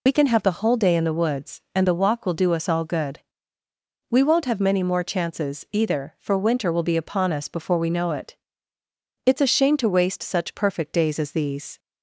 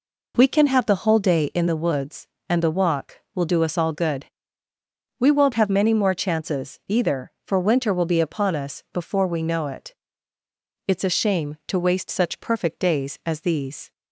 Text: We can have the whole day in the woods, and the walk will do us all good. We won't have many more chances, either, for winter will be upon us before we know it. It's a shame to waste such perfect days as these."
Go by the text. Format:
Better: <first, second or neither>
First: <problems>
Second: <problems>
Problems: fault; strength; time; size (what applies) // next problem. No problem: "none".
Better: second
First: loses the start of "We"; at 0.0 s; 50 ms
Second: none